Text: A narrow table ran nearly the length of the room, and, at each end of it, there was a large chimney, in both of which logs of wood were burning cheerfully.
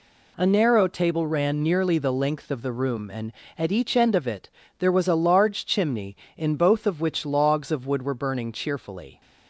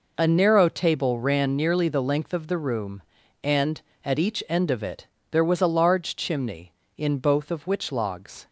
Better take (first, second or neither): first